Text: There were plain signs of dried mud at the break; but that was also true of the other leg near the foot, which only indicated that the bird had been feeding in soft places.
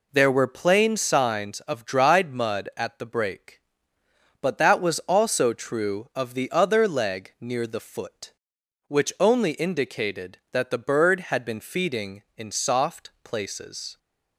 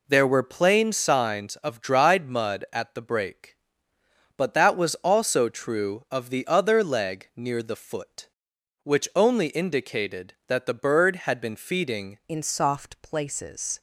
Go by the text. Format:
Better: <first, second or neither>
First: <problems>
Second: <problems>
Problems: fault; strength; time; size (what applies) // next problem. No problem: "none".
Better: first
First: none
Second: changes voice at "in"; from 12.2 s on; 1.6 s long